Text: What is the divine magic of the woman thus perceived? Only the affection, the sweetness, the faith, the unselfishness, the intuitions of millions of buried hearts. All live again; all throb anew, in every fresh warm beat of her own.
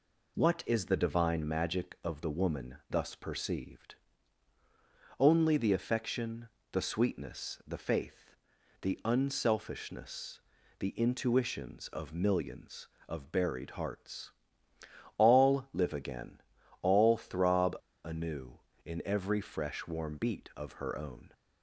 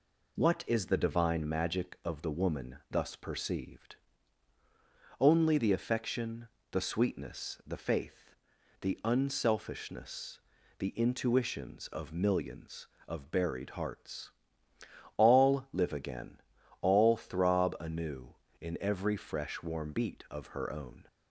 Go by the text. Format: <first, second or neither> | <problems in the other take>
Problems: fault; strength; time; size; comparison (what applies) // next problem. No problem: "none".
second | pauses between "throb" and "anew"; slight; at 17.7 s; 0.27 s long